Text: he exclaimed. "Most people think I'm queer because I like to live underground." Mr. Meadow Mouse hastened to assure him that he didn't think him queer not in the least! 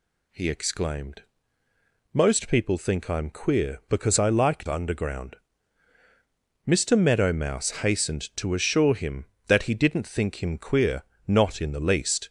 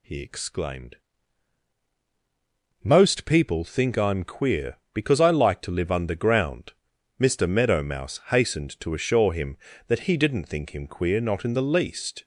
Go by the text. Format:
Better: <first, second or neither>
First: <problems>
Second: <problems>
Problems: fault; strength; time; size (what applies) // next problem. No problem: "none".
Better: second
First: skips "to live"; at 4.6 s // pauses between "queer" and "not"; slight; at 11.0 s; 0.24 s long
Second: none